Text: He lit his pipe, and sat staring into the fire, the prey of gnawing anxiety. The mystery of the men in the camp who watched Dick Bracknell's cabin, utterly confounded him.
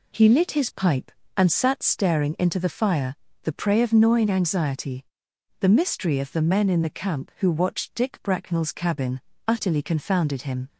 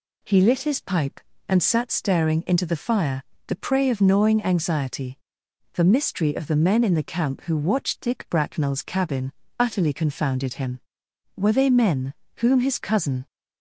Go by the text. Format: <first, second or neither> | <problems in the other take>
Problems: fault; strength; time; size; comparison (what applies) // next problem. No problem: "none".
first | goes on to say "Were they men whom his cousin"; strong; from 11.3 s on; 1.9 s long